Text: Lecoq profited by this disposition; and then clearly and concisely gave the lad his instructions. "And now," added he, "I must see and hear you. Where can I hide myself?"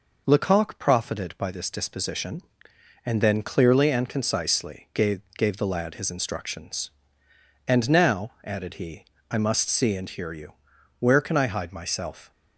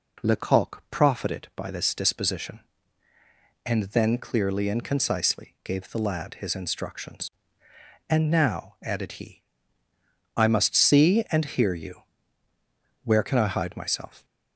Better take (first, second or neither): second